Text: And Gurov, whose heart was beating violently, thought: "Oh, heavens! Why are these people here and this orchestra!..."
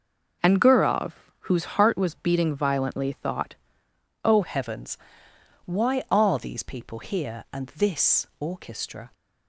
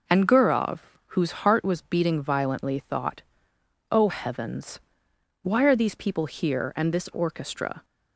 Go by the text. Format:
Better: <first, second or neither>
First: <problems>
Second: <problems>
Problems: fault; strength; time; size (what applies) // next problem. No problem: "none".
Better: second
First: starts louder than the rest; until 1.7 s; 6.5 dB // changes voice at "heavens"; from 4.4 s on; 4.6 s long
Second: none